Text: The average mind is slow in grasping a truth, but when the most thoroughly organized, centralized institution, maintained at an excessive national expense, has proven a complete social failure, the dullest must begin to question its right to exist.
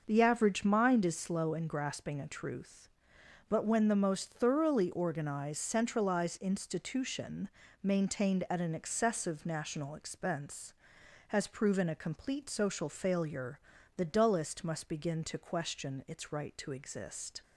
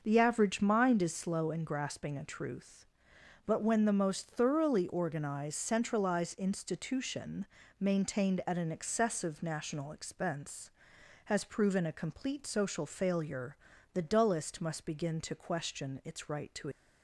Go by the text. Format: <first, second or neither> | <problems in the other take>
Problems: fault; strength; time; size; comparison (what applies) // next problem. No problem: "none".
first | starts louder than the rest; noticeable; until 1.0 s; 6 dB; noticeable in the first // stops before "exist"; at 16.7 s